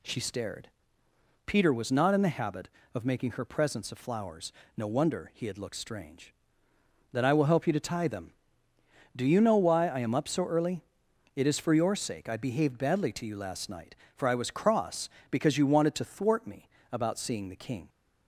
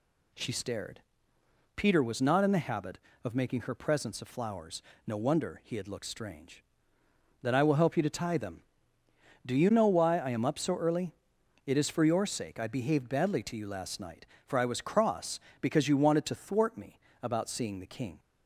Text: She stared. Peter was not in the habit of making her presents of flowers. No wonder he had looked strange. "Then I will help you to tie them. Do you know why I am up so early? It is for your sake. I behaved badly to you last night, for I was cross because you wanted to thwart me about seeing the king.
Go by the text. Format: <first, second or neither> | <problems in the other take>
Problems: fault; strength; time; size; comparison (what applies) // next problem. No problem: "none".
neither | pauses between "me" and "about"; slight; the same in both